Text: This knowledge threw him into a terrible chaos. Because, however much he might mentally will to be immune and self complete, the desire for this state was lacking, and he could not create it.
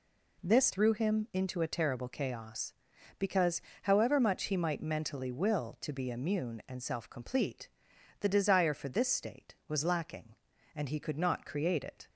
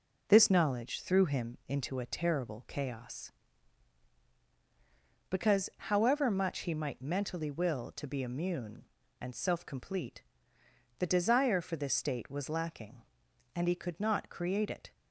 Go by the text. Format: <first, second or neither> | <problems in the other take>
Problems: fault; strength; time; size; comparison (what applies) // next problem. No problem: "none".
second | skips "knowledge"; at 0.7 s